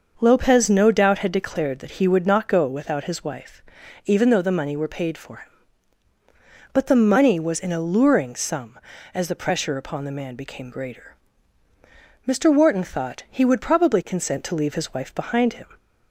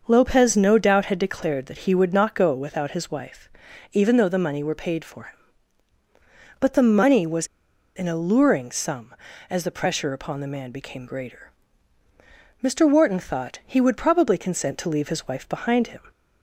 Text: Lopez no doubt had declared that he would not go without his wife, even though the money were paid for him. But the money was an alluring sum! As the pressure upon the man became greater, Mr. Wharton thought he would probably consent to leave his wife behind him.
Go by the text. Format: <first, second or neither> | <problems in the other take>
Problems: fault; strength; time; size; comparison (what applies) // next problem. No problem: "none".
first | starts louder than the rest; until 1.0 s; 6.5 dB; also in the first // pauses between "was" and "an"; noticeable; at 7.4 s; 0.48 s long